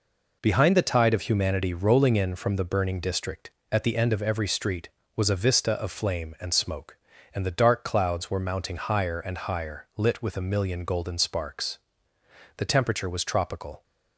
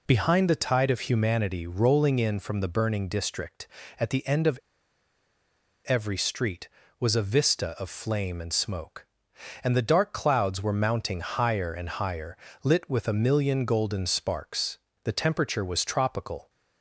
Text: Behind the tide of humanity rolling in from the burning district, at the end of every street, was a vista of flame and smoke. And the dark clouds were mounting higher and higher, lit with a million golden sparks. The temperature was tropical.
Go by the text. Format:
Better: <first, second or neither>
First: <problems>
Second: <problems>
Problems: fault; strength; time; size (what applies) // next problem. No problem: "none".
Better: first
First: none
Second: pauses between "of" and "every"; strong; at 4.5 s; 1.2 s long